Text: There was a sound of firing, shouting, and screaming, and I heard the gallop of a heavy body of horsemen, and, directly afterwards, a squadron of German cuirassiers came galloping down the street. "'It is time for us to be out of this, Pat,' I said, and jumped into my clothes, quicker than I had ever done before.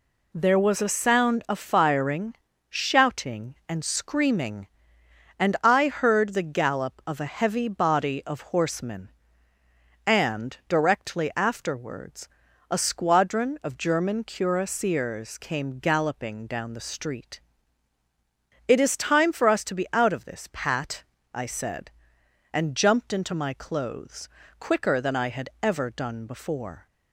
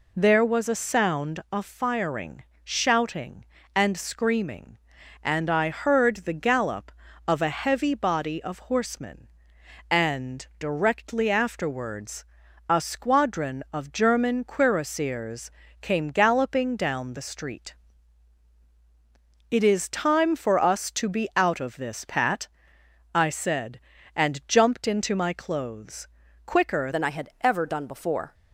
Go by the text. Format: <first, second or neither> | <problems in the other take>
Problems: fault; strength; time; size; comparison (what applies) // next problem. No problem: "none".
first | pauses between "cuirassiers" and "came"; slight; at 15.4 s; 0.32 s long // changes voice at "than"; from 26.9 s on; 1.4 s long